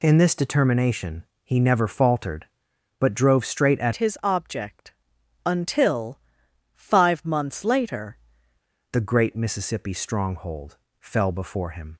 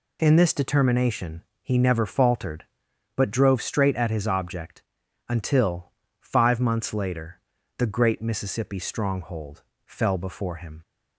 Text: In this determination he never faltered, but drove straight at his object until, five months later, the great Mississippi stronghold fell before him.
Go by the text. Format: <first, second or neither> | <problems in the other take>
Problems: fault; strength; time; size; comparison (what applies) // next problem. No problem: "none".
second | pauses between "determination" and "he"; slight; at 1.2 s; 0.22 s long; slight in the second // changes voice from "his" to "later"; from 3.9 to 8.1 s; 4.2 s long // pauses between "object" and "until"; noticeable; at 4.9 s; 0.54 s long; noticeable in the second // pauses between "stronghold" and "fell"; slight; at 10.7 s; 0.24 s long; slight in the second